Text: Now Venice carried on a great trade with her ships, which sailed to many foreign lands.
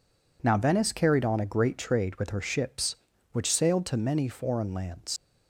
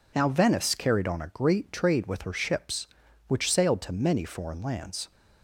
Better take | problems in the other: second | leaves "lands" unfinished; at 5.1 s; 65 ms

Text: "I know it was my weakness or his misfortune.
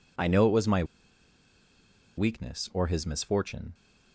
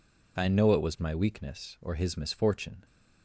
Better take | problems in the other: second | pauses between "my" and "weakness"; strong; at 0.8 s; 1.3 s long

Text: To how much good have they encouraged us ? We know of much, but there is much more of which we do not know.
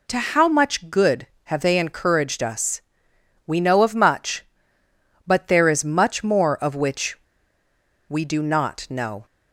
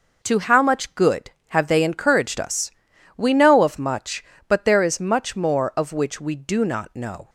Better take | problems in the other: second | pauses between "which" and "we"; noticeable; at 7.1 s; 0.91 s long

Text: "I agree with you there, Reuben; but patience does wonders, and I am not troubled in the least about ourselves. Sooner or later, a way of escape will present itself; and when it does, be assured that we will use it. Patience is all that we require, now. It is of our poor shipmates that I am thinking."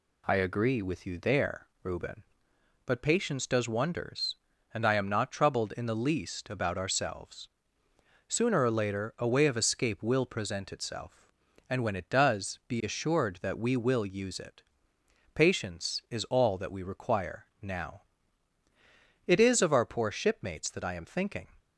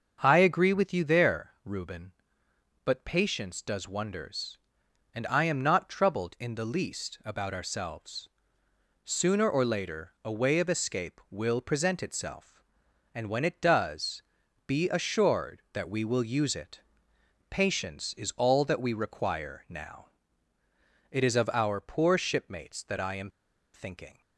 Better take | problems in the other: first | starts louder than the rest; until 1.2 s; 6.5 dB // pauses between "am" and "thinking"; at 23.2 s; 0.44 s long

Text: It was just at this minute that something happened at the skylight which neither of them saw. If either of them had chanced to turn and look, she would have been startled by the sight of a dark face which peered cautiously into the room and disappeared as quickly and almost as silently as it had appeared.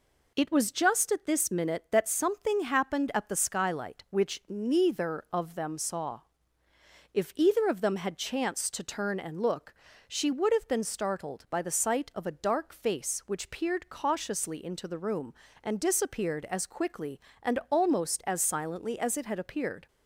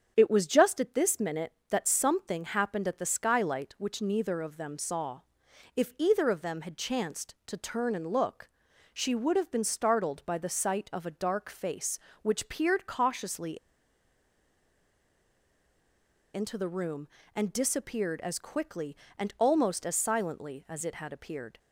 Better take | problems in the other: first | starts louder than the rest; strong; until 1.1 s; 8 dB // pauses between "cautiously" and "into"; strong; at 13.5 s; 2.7 s long

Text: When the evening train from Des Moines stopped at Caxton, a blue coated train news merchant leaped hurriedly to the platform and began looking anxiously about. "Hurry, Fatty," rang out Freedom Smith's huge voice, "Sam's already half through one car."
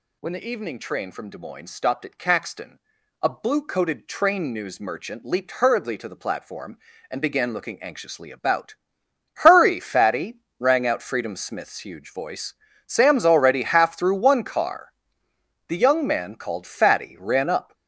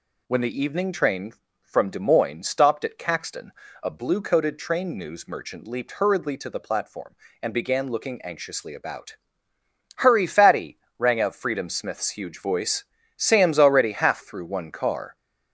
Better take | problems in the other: second | goes on to say "The young man called Fatty ran up"; strong; from 15.6 s on; 2.0 s long

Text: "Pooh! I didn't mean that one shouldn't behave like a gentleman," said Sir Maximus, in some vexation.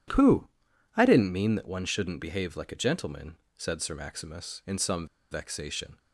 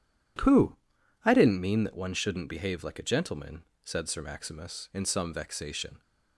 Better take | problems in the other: second | pauses between "some" and "vexation"; slight; at 5.0 s; 0.26 s long

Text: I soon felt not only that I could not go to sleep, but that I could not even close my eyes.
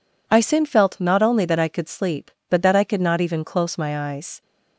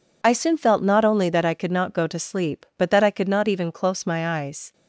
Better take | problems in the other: second | skips "not go to"; at 1.8 s

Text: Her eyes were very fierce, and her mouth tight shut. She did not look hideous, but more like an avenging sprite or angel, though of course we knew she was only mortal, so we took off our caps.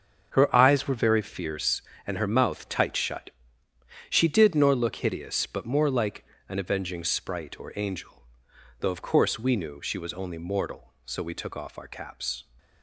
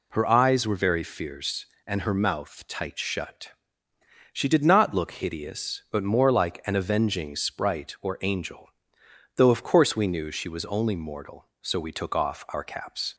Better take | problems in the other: second | starts louder than the rest; until 1.3 s; 6.5 dB // says "nor" for "not"; at 4.5 s // pauses between "like" and "an"; slight; at 6.2 s; 0.24 s long

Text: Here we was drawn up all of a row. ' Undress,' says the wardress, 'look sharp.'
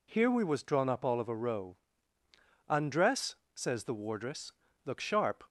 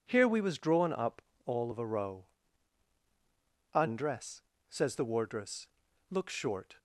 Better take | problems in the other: first | pauses between "up" and "all"; slight; at 1.2 s; 0.24 s long // says "short" for "sharp"; at 6.2 s

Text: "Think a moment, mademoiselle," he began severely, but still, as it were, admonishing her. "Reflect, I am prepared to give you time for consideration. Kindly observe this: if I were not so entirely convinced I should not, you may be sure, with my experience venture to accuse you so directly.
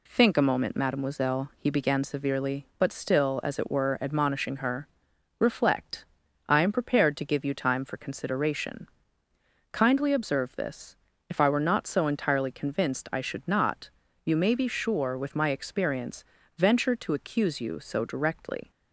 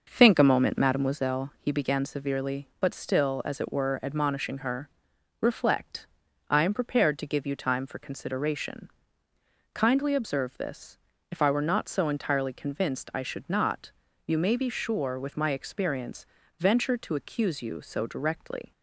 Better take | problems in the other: first | starts louder than the rest; noticeable; until 1.3 s; 6 dB // pauses between "experience" and "venture"; slight; at 16.2 s; 0.32 s long; slight in the first

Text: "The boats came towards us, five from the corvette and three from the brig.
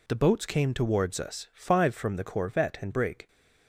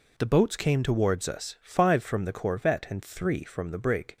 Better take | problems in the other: second | skips "three from the"; at 2.9 s

